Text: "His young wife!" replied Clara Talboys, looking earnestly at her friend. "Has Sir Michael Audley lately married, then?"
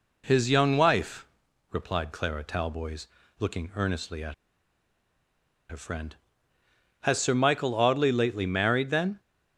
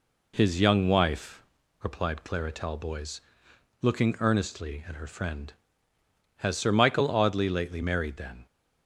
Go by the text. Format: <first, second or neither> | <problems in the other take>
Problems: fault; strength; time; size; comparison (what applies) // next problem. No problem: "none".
second | pauses between "at" and "her"; strong; at 4.3 s; 1.3 s long